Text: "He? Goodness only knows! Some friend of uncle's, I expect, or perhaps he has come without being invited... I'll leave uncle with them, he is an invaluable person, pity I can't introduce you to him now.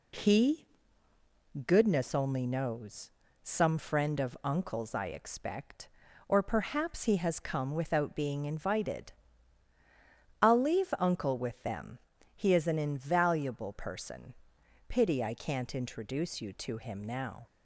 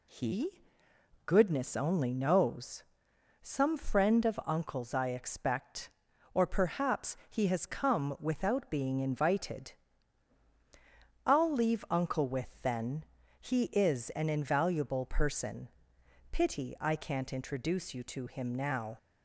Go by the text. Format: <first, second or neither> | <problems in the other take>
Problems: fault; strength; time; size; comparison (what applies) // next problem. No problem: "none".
first | says "then" for "them"; at 12.6 s